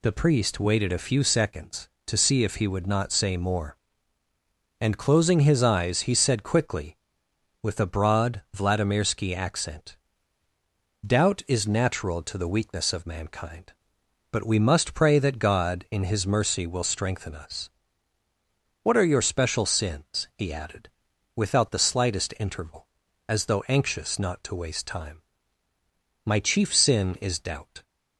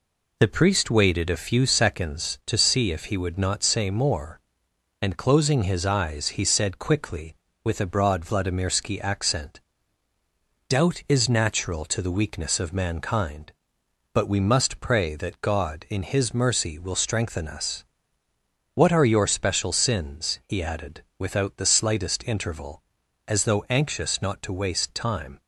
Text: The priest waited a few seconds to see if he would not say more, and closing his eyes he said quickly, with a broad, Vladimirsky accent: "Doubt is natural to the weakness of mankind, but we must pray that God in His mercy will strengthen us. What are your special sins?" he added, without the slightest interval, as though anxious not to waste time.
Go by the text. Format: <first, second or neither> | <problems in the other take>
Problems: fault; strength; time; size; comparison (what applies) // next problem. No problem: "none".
second | goes on to say "My chief sin is doubt"; from 26.2 s on; 1.5 s long